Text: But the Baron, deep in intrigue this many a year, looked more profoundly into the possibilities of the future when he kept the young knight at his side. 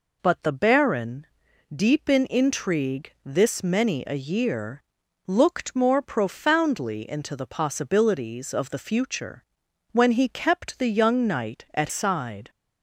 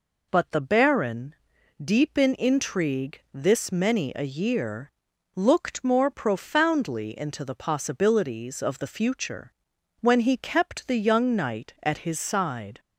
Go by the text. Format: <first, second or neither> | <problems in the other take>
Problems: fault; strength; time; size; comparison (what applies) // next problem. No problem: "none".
second | pauses between "future" and "when"; noticeable; at 9.4 s; 0.48 s long; noticeable in the second // skips "his"; at 11.8 s